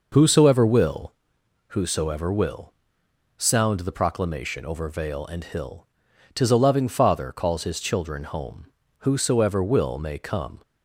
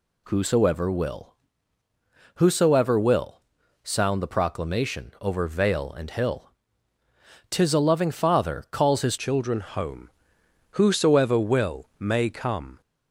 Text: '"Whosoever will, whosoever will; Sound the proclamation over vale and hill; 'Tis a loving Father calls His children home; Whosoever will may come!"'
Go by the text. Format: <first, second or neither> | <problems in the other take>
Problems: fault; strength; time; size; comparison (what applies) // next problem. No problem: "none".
first | changes voice at "children"; from 9.1 s on; 3.7 s long